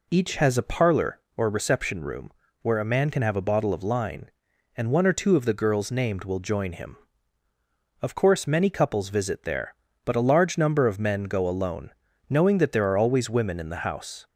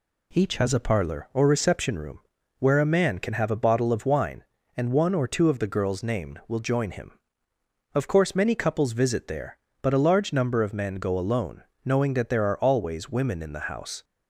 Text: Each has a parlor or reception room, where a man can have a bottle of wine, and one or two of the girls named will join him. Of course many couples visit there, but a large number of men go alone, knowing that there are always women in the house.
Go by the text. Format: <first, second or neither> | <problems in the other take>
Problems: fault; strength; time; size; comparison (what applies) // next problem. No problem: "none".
second | says "line" for "wine"; at 3.8 s